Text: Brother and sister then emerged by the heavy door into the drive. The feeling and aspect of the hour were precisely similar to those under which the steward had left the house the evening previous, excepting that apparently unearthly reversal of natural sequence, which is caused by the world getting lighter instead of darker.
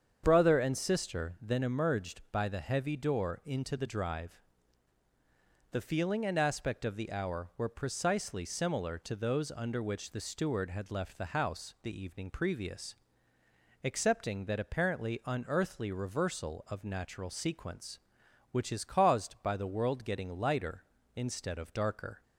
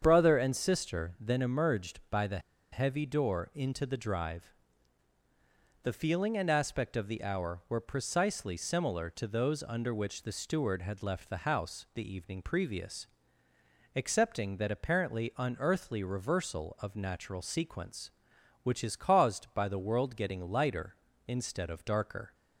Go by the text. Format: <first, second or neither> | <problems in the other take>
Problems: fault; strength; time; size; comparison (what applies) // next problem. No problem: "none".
first | starts louder than the rest; strong; until 1.0 s; 7.5 dB; strong in the first // pauses between "the" and "heavy"; slight; at 2.3 s; 0.33 s long